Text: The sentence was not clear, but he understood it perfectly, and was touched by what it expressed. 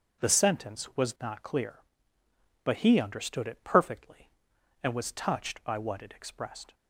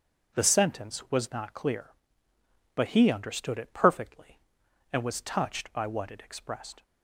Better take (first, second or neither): neither